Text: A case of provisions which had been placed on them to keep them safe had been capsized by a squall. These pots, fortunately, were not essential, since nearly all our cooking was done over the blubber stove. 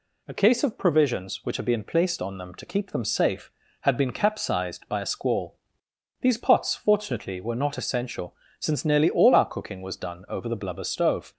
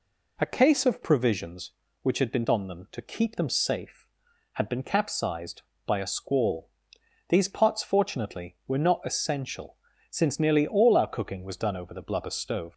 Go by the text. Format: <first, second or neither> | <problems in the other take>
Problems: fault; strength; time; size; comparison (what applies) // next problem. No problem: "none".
first | skips "placed"; at 2.4 s